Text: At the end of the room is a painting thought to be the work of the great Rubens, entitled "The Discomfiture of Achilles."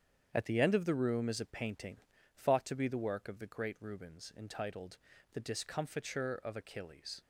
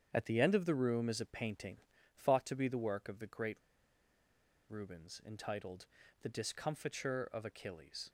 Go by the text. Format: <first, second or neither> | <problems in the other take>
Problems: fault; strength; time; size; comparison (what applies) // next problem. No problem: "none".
first | starts louder than the rest; strong; until 1.1 s; 8 dB; strong in the first // pauses between "painting" and "thought"; slight; at 1.8 s; 0.36 s long; slight in the first // pauses between "great" and "Rubens"; at 3.5 s; 1.1 s long // pauses between "entitled" and "The"; slight; at 5.8 s; 0.36 s long; slight in the first